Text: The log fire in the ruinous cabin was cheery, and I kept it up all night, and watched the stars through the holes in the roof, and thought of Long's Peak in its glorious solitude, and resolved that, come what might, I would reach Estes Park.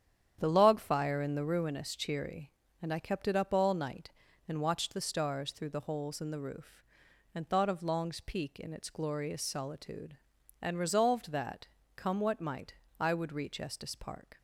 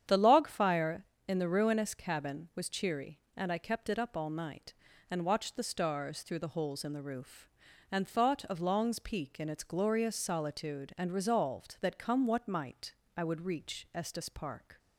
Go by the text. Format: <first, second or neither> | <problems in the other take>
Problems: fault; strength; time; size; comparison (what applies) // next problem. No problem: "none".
second | starts louder than the rest; strong; until 1.4 s; 9 dB; strong in the second // skips "cabin was"; at 1.9 s